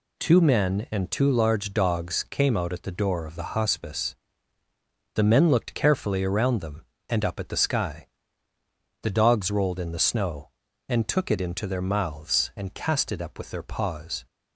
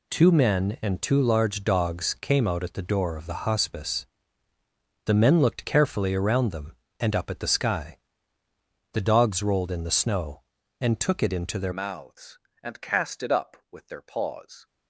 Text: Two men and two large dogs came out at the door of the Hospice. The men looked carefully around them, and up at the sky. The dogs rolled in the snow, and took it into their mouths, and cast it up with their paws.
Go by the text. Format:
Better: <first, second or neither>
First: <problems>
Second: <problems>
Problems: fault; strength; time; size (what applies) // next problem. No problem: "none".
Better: first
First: none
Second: changes voice at "mouths"; from 11.7 s on; 2.9 s long